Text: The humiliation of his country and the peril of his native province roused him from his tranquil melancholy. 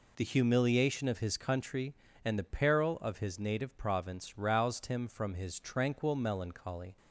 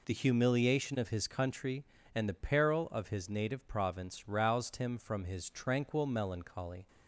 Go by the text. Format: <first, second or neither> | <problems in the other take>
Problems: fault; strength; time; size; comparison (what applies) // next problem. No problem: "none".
neither | none